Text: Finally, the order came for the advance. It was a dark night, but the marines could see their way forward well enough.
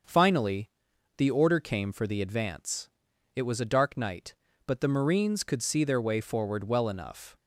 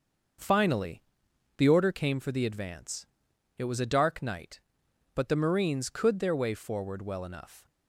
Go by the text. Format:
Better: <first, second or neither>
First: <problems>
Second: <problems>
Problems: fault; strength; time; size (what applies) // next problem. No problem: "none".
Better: first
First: starts louder than the rest; until 1.5 s; 6 dB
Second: starts louder than the rest; until 1.9 s; 6 dB // skips "see"; at 6.1 s